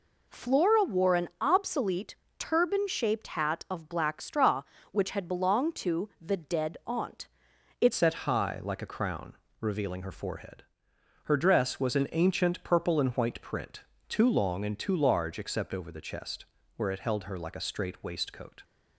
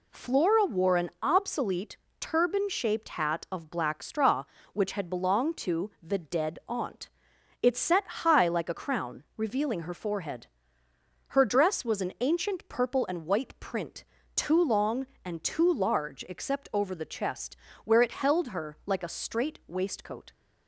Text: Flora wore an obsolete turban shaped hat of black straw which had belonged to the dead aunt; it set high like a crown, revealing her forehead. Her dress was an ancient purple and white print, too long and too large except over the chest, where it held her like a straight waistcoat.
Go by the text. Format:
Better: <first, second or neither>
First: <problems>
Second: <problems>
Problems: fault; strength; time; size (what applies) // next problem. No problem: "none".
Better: second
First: pauses between "obsolete" and "turban"; slight; at 2.1 s; 0.22 s long // changes voice at "set"; from 7.9 s on; 10.7 s long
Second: pauses between "obsolete" and "turban"; slight; at 1.9 s; 0.22 s long